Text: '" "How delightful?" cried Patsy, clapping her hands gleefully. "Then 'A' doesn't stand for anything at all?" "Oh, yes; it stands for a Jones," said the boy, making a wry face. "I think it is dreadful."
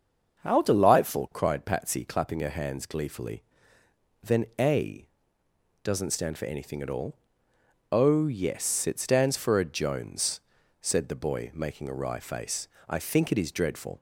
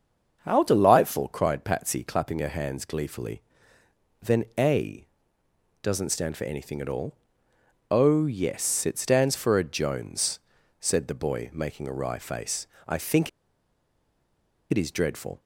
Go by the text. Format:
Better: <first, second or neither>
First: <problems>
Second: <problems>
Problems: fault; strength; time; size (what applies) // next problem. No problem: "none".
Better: first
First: starts louder than the rest; until 1.4 s; 6.5 dB // pauses between "A" and "doesn't"; noticeable; at 5.0 s; 0.78 s long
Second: starts louder than the rest; until 1.4 s; 6.5 dB // pauses between "A" and "doesn't"; noticeable; at 5.0 s; 0.78 s long // pauses between "think" and "it"; strong; at 13.2 s; 1.4 s long